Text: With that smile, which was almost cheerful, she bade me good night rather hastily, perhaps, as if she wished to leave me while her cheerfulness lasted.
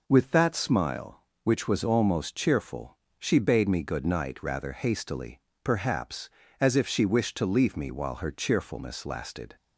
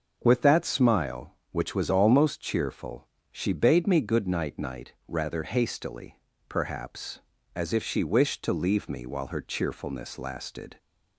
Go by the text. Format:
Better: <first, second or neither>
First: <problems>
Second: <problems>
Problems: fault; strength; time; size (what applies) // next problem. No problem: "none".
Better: first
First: none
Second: starts louder than the rest; until 1.2 s; 6 dB // says "night" twice; at 4.5 s